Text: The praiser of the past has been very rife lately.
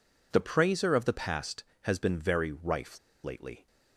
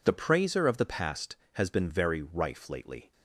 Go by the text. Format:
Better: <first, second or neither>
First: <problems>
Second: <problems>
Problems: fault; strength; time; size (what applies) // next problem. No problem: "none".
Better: second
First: pauses between "rife" and "lately"; slight; at 2.9 s; 0.25 s long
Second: none